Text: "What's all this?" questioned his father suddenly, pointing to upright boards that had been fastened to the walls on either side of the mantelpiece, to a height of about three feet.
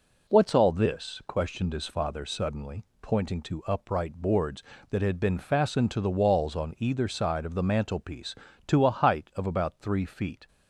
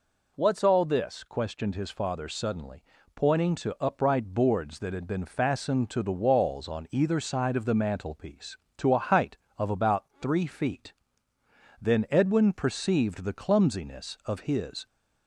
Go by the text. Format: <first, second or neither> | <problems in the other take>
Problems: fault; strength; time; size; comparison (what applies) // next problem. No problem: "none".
first | pauses between "about" and "three"; slight; at 10.0 s; 0.16 s long // goes on to say "Then Edwin perceived the clumsiness of his"; strong; from 11.8 s on; 3.0 s long